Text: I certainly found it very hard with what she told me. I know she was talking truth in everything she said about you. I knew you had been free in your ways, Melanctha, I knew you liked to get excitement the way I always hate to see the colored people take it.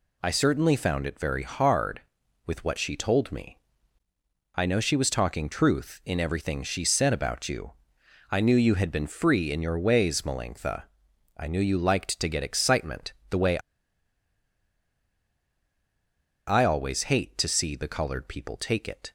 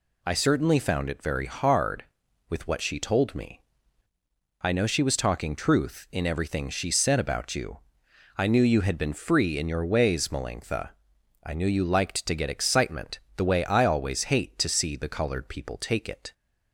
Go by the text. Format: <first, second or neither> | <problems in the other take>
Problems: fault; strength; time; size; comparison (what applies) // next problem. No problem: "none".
second | pauses between "excitement" and "the"; slight; at 13.1 s; 0.18 s long; slight in the second // pauses between "way" and "I"; strong; at 13.5 s; 2.8 s long